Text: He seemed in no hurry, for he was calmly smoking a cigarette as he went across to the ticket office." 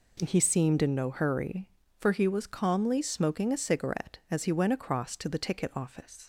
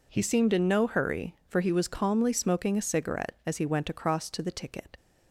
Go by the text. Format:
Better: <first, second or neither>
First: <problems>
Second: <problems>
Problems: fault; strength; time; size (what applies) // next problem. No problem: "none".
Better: first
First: none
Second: stops before "office"; at 4.9 s